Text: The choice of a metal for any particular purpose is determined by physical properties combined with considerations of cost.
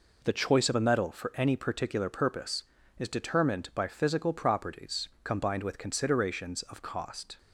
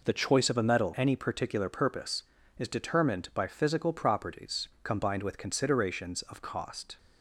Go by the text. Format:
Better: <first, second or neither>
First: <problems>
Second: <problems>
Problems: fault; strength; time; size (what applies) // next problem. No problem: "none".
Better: first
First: pauses between "properties" and "combined"; slight; at 5.0 s; 0.16 s long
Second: skips "for"; at 0.9 s // pauses between "properties" and "combined"; slight; at 4.6 s; 0.16 s long